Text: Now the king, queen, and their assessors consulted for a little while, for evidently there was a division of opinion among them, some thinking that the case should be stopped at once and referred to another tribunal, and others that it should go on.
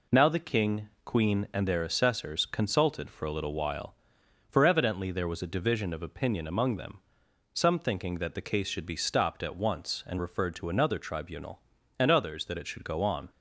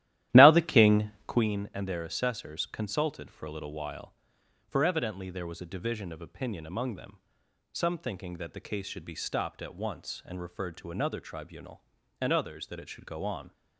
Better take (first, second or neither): first